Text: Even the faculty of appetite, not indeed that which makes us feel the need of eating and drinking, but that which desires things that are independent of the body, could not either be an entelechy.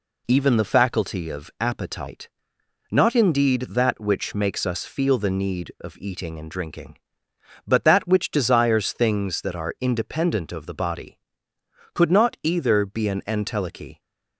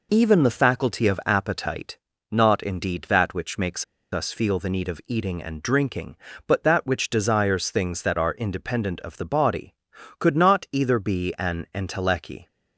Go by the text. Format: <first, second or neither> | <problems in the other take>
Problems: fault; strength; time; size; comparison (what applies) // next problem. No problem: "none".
first | pauses between "makes" and "us"; slight; at 3.8 s; 0.28 s long